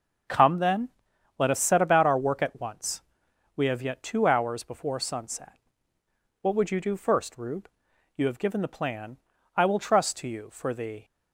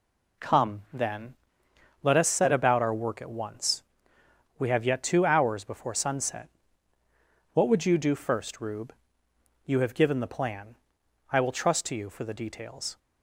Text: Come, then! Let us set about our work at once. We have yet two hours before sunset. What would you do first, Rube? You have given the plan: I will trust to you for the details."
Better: second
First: starts louder than the rest; until 1.7 s; 7 dB // stops before "details"; at 11.0 s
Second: none

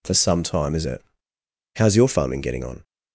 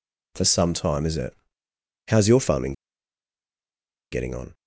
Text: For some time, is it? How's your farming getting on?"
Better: first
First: none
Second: pauses between "farming" and "getting"; strong; at 2.7 s; 1.3 s long

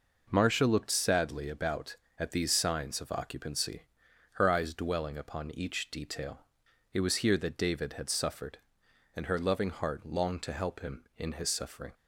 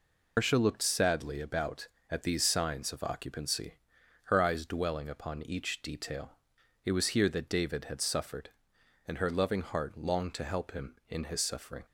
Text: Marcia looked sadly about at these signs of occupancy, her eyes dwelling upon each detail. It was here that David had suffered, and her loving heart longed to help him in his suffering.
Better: first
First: none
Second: loses the start of "Marcia"; at 0.3 s; 180 ms

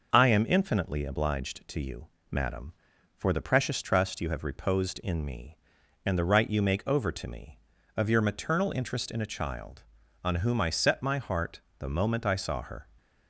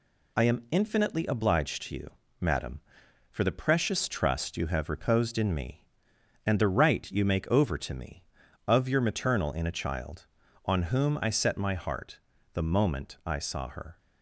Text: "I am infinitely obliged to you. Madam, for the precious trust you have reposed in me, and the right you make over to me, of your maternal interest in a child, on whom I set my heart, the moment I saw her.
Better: first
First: none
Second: skips "interest"; at 9.5 s

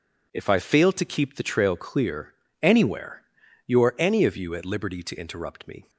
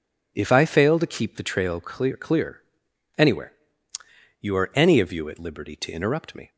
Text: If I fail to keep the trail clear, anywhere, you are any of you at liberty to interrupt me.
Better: first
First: none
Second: says "clear" twice; at 2.1 s

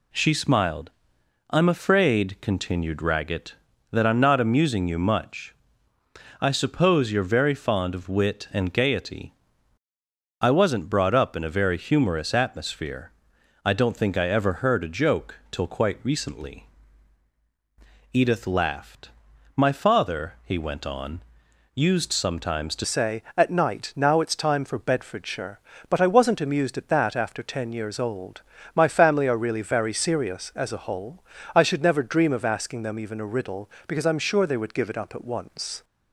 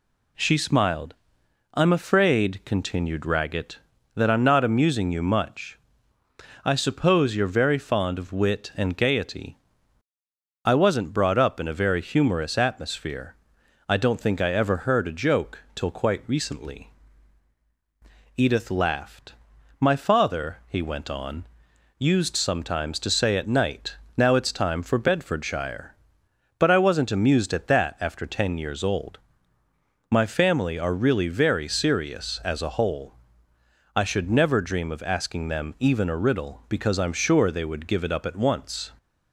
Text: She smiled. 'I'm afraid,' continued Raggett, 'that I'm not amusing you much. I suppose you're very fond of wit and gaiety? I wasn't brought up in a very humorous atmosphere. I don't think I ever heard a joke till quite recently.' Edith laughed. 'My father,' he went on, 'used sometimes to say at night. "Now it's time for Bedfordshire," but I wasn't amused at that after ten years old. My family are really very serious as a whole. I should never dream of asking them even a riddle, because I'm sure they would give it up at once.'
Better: second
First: changes voice at "say"; from 22.8 s on; 13.0 s long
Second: none

